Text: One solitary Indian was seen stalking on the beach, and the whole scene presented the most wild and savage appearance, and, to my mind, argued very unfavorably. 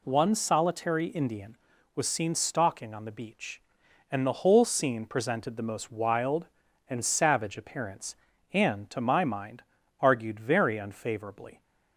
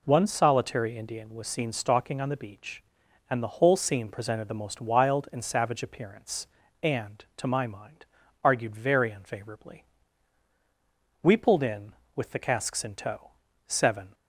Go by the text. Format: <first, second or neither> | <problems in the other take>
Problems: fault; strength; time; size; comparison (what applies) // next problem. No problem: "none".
first | goes on to say "We pulled in with the casks in tow seven"; strong; from 11.2 s on; 2.9 s long